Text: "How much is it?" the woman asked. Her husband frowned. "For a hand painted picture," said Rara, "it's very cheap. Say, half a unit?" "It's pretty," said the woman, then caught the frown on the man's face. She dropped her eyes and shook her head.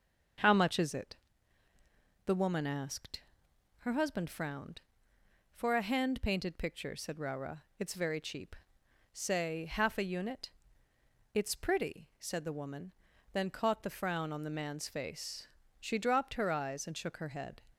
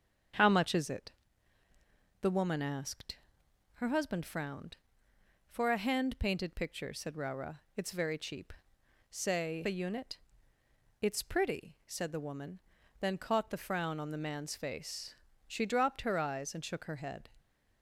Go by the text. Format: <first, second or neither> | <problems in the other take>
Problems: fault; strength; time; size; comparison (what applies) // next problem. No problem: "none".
first | starts louder than the rest; strong; until 2.4 s; 7.5 dB; also in the first // skips "half"; at 9.6 s